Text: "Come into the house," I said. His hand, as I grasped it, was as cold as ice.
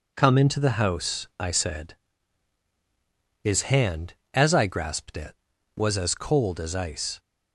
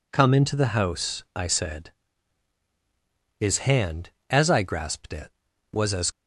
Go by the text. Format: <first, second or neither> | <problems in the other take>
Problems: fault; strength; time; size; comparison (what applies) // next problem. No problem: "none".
first | stops before "cold as ice"; at 6.1 s